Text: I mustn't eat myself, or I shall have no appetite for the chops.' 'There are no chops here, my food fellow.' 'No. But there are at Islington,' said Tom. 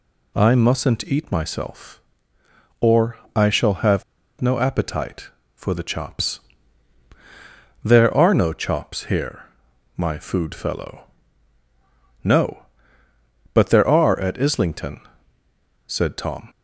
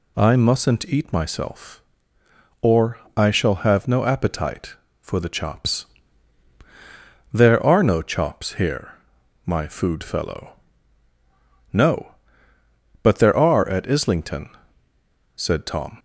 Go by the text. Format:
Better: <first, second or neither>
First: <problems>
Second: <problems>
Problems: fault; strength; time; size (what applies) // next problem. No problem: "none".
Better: second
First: pauses between "or" and "I"; slight; at 3.1 s; 0.18 s long // pauses between "have" and "no"; at 4.0 s; 0.37 s long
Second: pauses between "or" and "I"; slight; at 2.9 s; 0.18 s long